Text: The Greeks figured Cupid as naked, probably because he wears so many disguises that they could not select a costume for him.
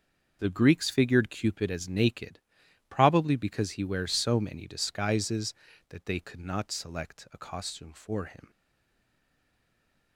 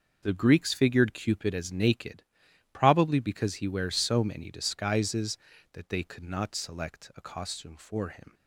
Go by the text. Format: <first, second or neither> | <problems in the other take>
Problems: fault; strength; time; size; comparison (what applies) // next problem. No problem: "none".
second | starts louder than the rest; noticeable; until 1.4 s; 6 dB; noticeable in the second // stays silent after the last word; noticeable; from 8.5 s on; 1.6 s long